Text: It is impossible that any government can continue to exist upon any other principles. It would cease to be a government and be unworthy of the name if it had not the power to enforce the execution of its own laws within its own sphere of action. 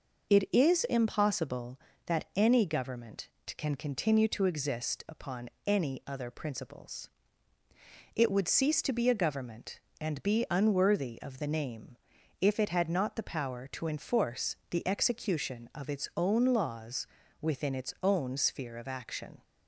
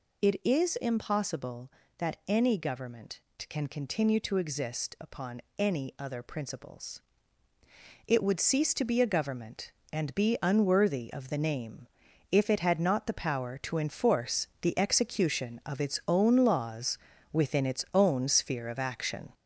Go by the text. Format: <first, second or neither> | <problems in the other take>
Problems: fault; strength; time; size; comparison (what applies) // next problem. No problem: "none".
first | gets louder; noticeable; throughout; 5 dB // pauses between "upon" and "any"; slight; at 5.4 s; 0.16 s long; slight in the first // pauses between "name" and "if"; at 11.8 s; 0.44 s long; also in the first // pauses between "laws" and "within"; slight; at 16.9 s; 0.36 s long; slight in the first